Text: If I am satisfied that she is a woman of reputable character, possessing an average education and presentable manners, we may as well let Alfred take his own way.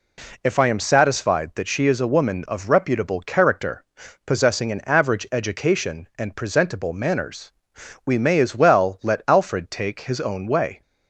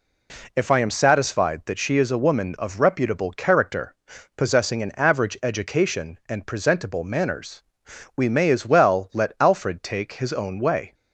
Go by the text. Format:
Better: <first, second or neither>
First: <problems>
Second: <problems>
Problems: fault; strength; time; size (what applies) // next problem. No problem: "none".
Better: neither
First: none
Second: none